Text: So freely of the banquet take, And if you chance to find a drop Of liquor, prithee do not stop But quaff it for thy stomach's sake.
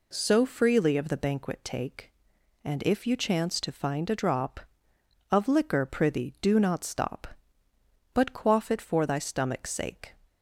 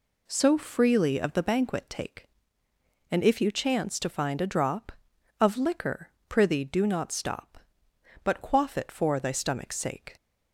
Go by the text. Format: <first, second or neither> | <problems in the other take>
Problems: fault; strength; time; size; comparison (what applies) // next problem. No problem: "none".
neither | none